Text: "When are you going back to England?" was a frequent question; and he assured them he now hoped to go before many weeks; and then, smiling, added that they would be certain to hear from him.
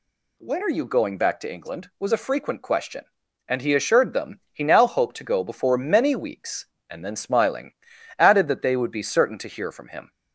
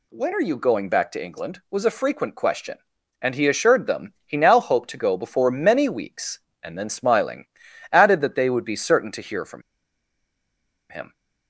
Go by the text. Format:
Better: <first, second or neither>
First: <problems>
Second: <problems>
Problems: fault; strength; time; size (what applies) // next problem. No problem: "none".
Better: first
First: none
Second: pauses between "from" and "him"; strong; at 9.6 s; 1.3 s long